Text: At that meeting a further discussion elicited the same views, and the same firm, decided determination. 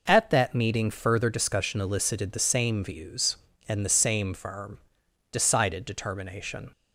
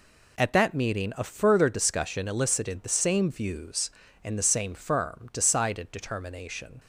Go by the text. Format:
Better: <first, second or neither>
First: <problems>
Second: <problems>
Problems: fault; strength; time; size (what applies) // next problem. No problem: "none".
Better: second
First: skips "a"; at 0.8 s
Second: none